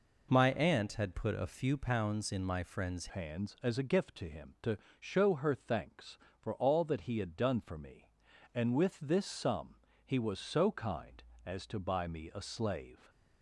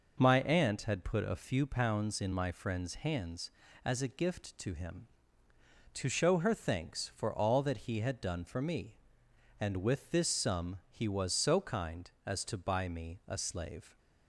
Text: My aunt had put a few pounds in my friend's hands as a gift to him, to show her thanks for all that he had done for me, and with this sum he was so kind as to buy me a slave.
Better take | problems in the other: second | changes voice at "hands"; from 3.0 s on; 10.0 s long // pauses between "to" and "show"; slight; at 4.7 s; 0.22 s long // pauses between "sum" and "he"; slight; at 9.7 s; 0.24 s long

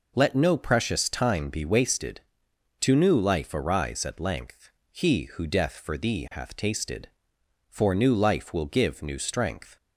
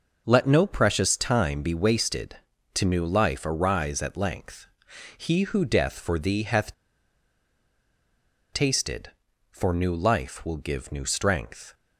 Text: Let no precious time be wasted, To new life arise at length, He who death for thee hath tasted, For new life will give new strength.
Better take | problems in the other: first | pauses between "hath" and "tasted"; strong; at 6.7 s; 1.7 s long

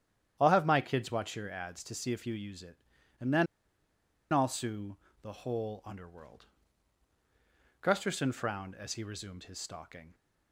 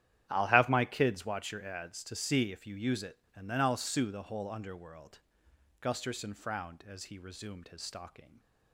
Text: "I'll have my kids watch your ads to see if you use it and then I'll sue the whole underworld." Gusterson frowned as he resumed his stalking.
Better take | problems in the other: second | starts louder than the rest; strong; until 1.4 s; 10 dB; strong in the second // pauses between "then" and "I'll"; noticeable; at 3.4 s; 0.86 s long // pauses between "sue" and "the"; slight; at 4.9 s; 0.24 s long

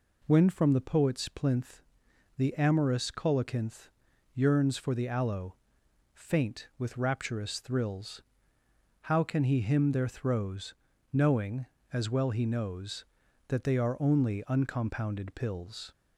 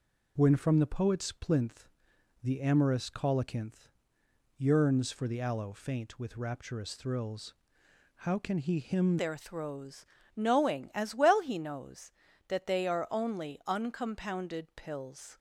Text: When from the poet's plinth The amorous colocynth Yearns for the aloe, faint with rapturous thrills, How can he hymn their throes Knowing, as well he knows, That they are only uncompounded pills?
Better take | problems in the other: first | pauses between "plinth" and "The"; noticeable; at 1.8 s; 0.54 s long; noticeable in the first // pauses between "colocynth" and "Yearns"; noticeable; at 3.8 s; 0.70 s long; noticeable in the first // changes voice at "their"; from 9.1 s on; 6.2 s long // pauses between "throes" and "Knowing"; slight; at 10.0 s; 0.32 s long; slight in the first

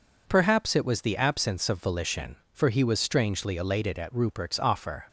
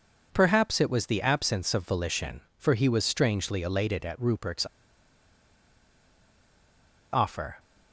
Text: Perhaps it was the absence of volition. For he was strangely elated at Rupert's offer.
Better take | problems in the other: first | pauses between "Rupert's" and "offer"; strong; at 4.6 s; 2.4 s long

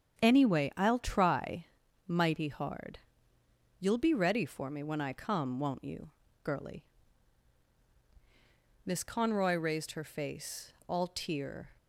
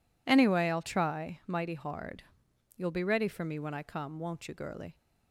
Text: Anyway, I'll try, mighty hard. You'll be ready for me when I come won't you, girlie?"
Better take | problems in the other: second | starts louder than the rest; strong; until 1.3 s; 8.5 dB // goes on to say "Miss Conroy raised her face all tear"; strong; from 8.8 s on; 2.8 s long

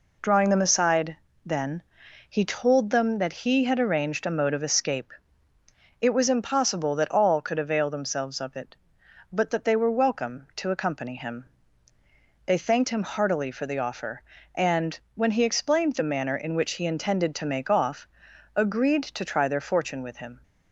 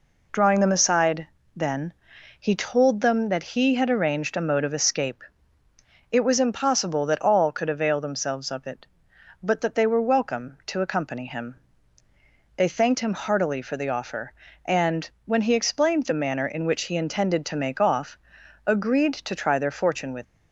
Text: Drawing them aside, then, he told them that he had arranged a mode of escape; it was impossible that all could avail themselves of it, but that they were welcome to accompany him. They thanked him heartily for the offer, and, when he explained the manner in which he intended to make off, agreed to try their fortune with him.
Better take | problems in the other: first | stops before "him"; at 20.2 s

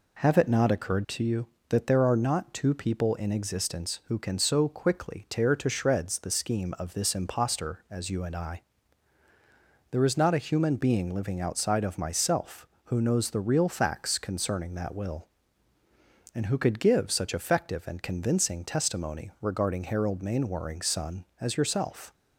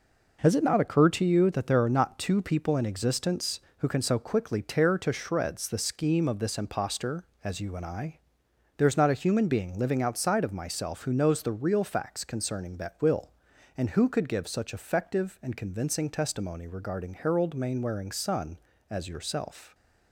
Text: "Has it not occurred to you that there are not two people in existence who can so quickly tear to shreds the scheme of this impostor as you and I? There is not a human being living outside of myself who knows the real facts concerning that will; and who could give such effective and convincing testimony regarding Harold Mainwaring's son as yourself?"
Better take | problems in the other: second | says "Have" for "Has"; at 0.2 s

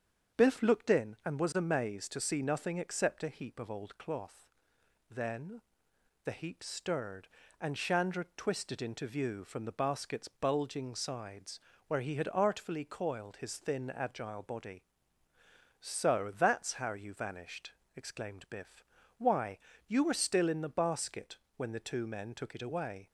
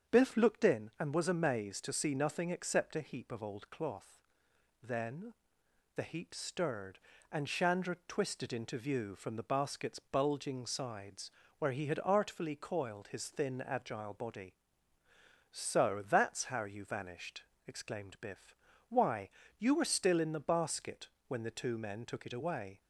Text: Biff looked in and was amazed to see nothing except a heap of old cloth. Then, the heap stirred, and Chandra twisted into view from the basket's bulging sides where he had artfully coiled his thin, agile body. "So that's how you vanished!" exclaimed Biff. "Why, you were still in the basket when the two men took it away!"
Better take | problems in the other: neither | starts louder than the rest; strong; the same in both // pauses between "sides" and "where"; slight; the same in both // pauses between "basket" and "when"; slight; the same in both

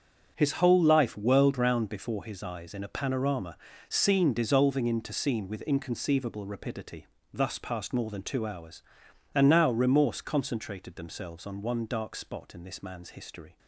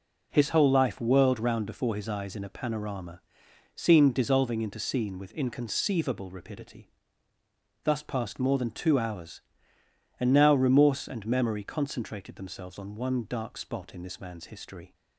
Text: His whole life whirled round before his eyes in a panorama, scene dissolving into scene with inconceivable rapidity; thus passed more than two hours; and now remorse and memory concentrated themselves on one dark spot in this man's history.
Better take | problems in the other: second | starts louder than the rest; strong; until 1.3 s; 7.5 dB // skips "and memory"; at 10.2 s

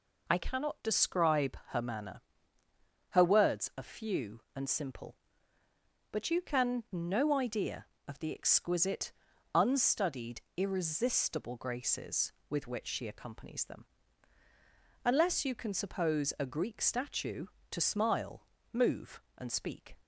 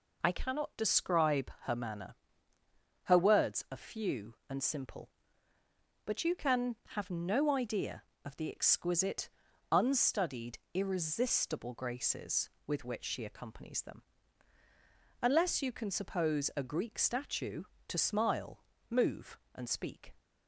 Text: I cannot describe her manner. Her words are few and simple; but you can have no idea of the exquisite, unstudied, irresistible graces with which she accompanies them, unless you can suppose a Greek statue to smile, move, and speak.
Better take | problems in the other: second | skips "have"; at 6.8 s

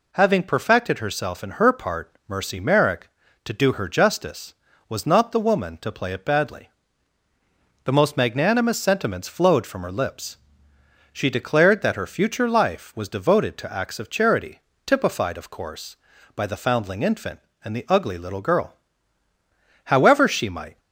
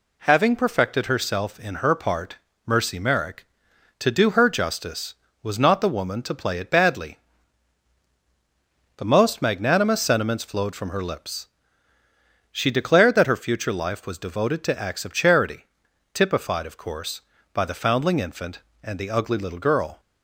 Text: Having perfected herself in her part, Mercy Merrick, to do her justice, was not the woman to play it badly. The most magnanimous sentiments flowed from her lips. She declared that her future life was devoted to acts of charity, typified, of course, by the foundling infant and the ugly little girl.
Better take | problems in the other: second | goes on to say "However she might"; noticeable; from 19.8 s on; 0.94 s long

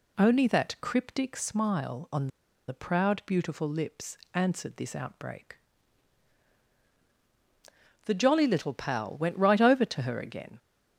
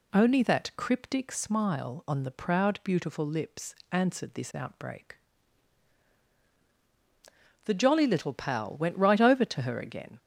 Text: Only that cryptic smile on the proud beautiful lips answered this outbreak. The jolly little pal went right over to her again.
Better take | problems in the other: second | pauses between "on" and "the"; at 2.2 s; 0.39 s long // pauses between "lips" and "answered"; slight; at 4.1 s; 0.16 s long; slight in the second

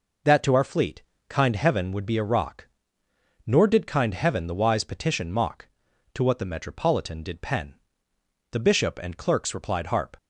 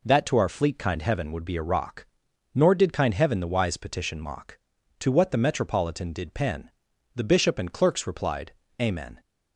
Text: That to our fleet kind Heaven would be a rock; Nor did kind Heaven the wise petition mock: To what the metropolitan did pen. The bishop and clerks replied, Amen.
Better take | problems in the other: second | pauses between "fleet" and "kind"; slight; at 1.0 s; 0.26 s long // says "Harp" for "Amen"; at 9.8 s

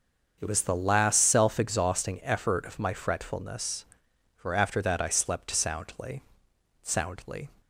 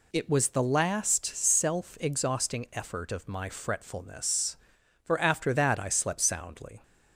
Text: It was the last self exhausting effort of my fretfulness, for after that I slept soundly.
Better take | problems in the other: second | starts louder than the rest; until 1.4 s; 6.5 dB // says "soundly" twice; at 6.8 s

